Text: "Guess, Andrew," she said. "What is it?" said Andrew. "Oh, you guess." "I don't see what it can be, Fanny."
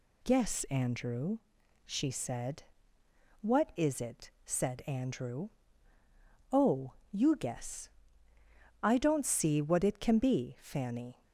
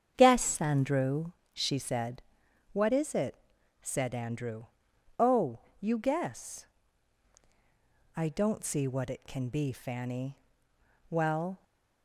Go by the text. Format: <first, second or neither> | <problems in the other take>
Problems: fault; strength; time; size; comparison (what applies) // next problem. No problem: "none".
first | starts louder than the rest; strong; until 1.1 s; 8 dB // goes on to say "Well"; from 11.0 s on; 0.54 s long